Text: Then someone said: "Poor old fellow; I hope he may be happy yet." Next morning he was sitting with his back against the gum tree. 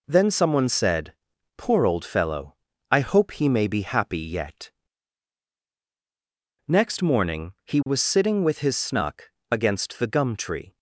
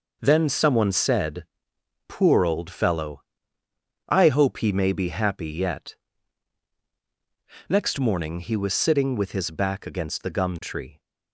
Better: second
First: says "snuck" for "back"; at 8.7 s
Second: none

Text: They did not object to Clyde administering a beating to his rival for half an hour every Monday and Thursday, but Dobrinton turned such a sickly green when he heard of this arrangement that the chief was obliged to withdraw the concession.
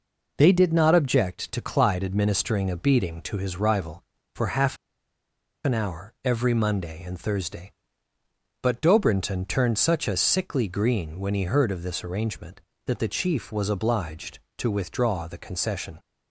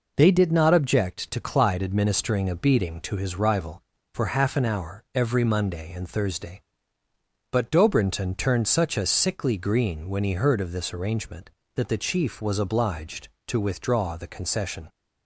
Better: second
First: pauses between "half" and "an"; noticeable; at 4.7 s; 0.89 s long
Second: none

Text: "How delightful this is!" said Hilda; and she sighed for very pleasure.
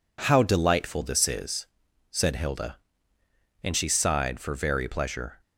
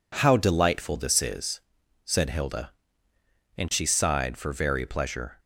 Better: neither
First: none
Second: none

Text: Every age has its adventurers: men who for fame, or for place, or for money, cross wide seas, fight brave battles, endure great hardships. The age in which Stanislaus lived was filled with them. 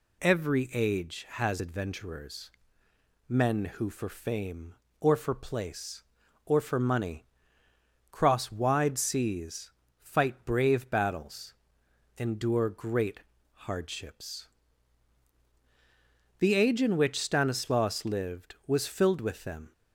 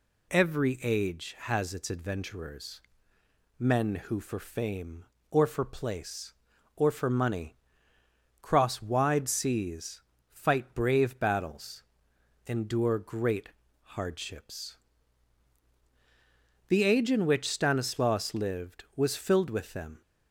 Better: second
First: skips "its"; at 1.5 s // pauses between "great" and "hardships"; at 13.2 s; 0.44 s long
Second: pauses between "great" and "hardships"; at 13.5 s; 0.44 s long

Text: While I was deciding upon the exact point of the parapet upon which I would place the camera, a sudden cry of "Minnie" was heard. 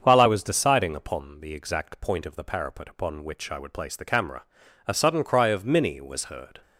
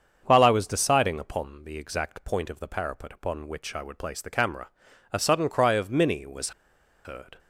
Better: first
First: starts louder than the rest; until 1.0 s; 7 dB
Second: starts louder than the rest; until 1.2 s; 7 dB // pauses between "was" and "heard"; noticeable; at 6.5 s; 0.54 s long

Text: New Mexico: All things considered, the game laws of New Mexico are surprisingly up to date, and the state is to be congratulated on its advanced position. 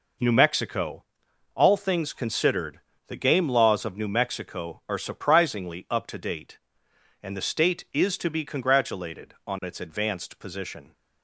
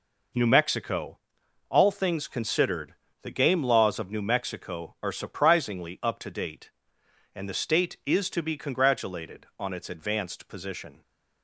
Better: neither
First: none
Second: none

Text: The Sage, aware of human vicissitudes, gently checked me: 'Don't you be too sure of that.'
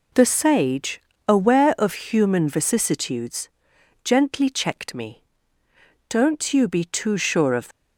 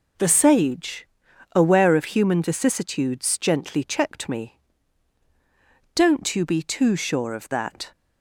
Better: second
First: stops before "that"; at 7.7 s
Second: none

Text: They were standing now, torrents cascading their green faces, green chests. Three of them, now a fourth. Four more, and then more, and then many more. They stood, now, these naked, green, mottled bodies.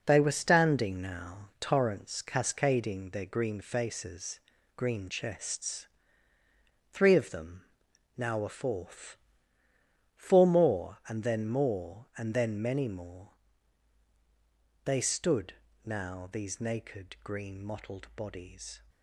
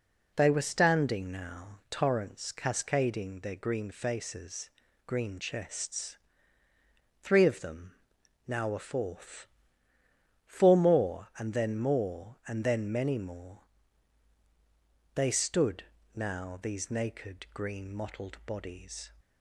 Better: second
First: gets quieter; throughout; 7 dB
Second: none

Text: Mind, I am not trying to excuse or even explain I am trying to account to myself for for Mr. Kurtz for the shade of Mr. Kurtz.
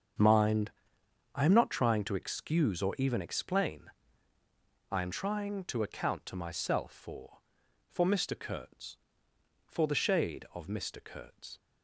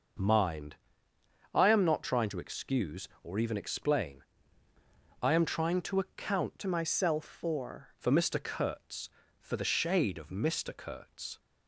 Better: first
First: starts louder than the rest; until 1.8 s; 7 dB // pauses between "explain" and "I"; at 3.9 s; 1.0 s long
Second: starts louder than the rest; noticeable; until 2.0 s; 6 dB // pauses between "explain" and "I"; noticeable; at 4.2 s; 0.98 s long // changes voice from "myself" to "for"; from 6.6 to 7.9 s; 1.3 s long

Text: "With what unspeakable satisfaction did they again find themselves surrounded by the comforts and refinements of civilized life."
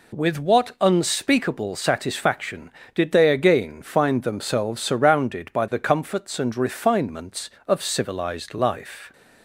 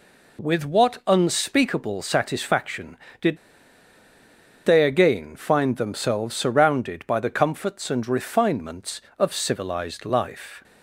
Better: first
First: none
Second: pauses between "did" and "they"; strong; at 3.3 s; 1.2 s long

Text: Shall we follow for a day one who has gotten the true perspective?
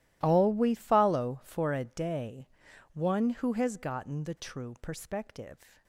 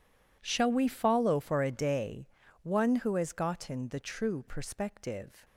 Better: second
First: starts louder than the rest; strong; until 1.2 s; 15 dB // says "All" for "Shall"; at 0.2 s // pauses between "day" and "one"; noticeable; at 2.4 s; 0.48 s long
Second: pauses between "day" and "one"; slight; at 2.2 s; 0.36 s long

